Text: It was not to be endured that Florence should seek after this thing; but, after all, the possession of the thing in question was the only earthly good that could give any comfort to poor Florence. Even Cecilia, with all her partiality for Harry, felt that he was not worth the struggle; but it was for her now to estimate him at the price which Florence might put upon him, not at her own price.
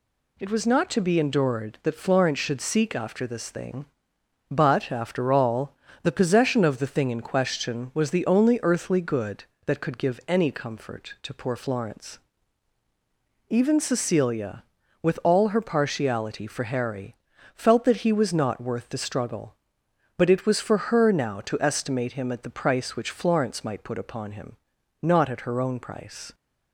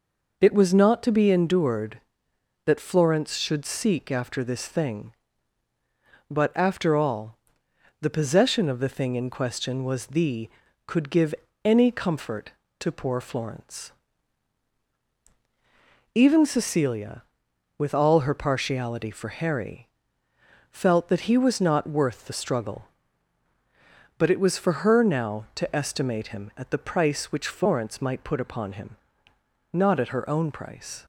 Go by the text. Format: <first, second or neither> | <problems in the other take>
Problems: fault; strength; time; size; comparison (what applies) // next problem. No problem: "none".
first | skips "only earthly good that"; at 10.6 s // pauses between "give" and "any"; slight; at 11.3 s; 0.32 s long